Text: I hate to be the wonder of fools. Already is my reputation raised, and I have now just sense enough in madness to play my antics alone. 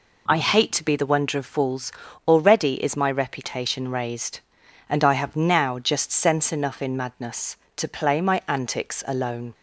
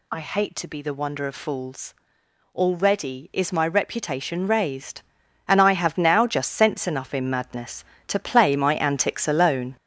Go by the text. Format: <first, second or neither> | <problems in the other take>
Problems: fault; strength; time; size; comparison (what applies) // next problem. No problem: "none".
first | gets louder; noticeable; throughout; 6 dB